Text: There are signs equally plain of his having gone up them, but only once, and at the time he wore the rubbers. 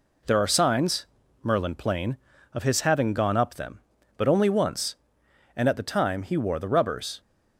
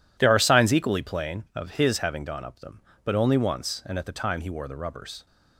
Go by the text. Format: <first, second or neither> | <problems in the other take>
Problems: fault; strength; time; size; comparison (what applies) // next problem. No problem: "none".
second | says "merlin" for "equally"; at 1.4 s